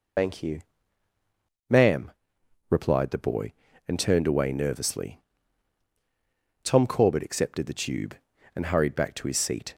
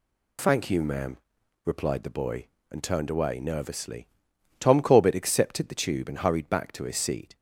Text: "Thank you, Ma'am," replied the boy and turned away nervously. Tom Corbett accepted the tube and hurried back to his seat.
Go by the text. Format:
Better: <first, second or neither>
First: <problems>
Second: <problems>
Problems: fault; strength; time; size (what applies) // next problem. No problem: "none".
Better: second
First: loses the start of "Thank"; at 0.1 s; 60 ms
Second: none